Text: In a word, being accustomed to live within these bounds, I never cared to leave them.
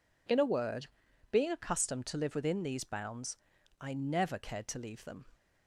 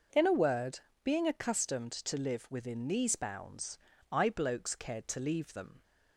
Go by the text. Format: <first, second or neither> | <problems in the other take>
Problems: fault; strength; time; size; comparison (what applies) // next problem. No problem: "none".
first | says "blokes" for "never"; at 4.2 s